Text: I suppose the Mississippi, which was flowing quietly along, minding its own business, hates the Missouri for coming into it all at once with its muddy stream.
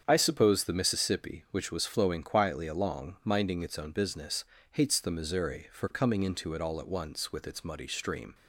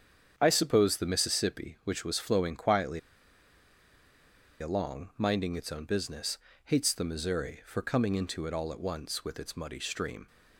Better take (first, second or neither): first